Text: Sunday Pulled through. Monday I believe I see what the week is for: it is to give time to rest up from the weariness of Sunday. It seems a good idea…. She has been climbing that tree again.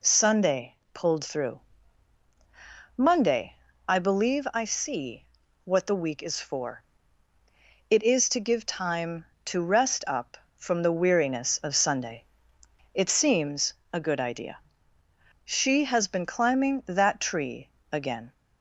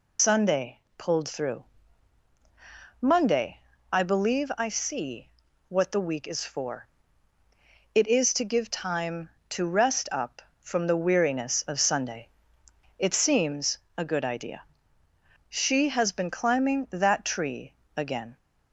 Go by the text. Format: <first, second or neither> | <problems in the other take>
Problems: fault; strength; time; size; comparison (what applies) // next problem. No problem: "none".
first | loses the start of "Sunday"; at 0.1 s; 120 ms // pauses between "Sunday" and "Pulled"; slight; at 0.7 s; 0.18 s long; slight in the first // pauses between "Monday" and "I"; slight; at 3.5 s; 0.32 s long; slight in the first // pauses between "see" and "what"; slight; at 5.3 s; 0.36 s long; slight in the first // pauses between "seems" and "a"; slight; at 13.7 s; 0.18 s long; slight in the first // pauses between "tree" and "again"; slight; at 17.7 s; 0.24 s long; slight in the first